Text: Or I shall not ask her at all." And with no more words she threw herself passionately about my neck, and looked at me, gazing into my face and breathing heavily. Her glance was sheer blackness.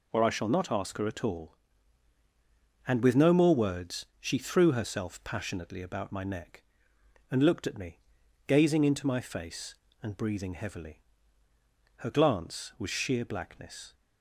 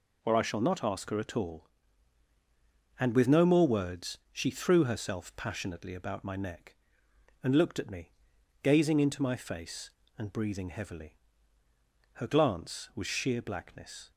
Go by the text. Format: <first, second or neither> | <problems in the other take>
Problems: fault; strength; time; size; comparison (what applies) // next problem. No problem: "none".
neither | none